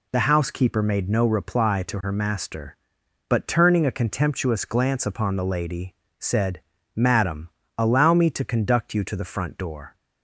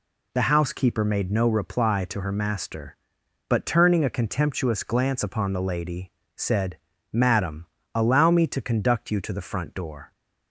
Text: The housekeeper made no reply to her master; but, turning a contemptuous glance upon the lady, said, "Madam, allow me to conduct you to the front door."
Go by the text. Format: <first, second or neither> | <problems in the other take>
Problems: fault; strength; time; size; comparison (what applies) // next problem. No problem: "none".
neither | none